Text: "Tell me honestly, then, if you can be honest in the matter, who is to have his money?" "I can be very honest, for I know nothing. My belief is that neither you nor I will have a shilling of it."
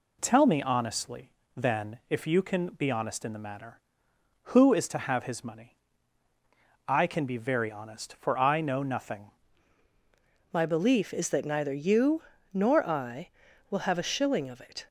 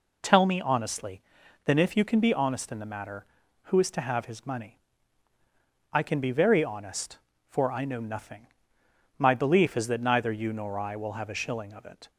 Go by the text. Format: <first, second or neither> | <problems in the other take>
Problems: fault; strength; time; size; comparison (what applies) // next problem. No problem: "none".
second | changes voice at "My"; from 10.5 s on; 4.3 s long // pauses between "you" and "nor"; slight; at 12.2 s; 0.30 s long